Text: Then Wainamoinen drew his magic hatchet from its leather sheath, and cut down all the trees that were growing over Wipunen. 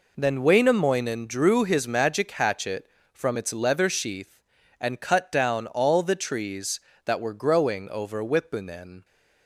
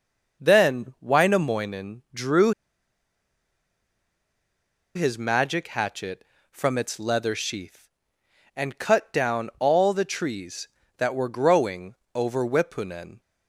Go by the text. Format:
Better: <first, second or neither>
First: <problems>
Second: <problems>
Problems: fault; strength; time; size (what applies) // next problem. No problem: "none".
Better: first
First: none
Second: pauses between "drew" and "his"; strong; at 2.5 s; 2.4 s long // pauses between "growing" and "over"; slight; at 11.9 s; 0.20 s long